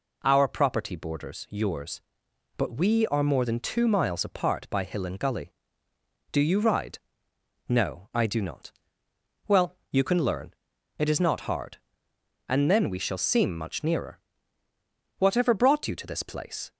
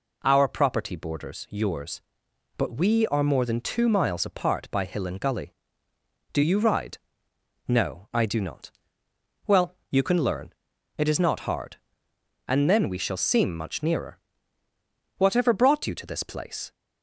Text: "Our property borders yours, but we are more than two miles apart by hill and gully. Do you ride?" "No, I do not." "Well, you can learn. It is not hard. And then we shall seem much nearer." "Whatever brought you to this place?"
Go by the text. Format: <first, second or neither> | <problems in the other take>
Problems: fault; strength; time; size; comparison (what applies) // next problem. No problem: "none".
neither | none